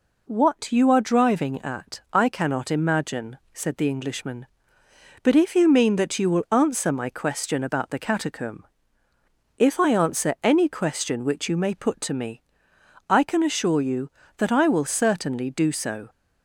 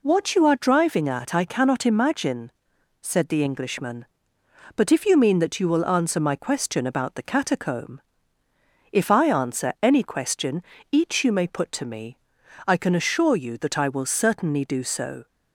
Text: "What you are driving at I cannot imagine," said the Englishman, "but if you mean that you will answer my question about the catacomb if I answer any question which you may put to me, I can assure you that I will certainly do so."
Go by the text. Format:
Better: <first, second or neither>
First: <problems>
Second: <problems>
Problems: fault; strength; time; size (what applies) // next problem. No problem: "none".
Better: first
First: pauses between "catacomb" and "if"; noticeable; at 8.6 s; 0.94 s long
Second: pauses between "catacomb" and "if"; noticeable; at 8.0 s; 0.92 s long // says "each" for "which"; at 10.9 s